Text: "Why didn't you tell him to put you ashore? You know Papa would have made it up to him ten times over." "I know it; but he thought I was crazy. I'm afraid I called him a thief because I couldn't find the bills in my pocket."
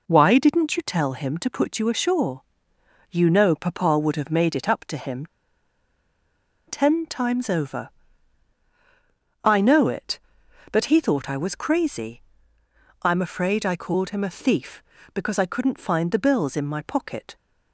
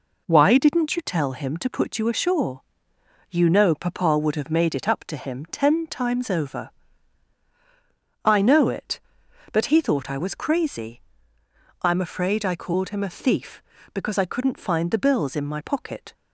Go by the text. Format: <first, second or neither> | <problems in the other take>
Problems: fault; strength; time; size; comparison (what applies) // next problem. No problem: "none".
second | pauses between "him" and "ten"; strong; at 5.2 s; 1.4 s long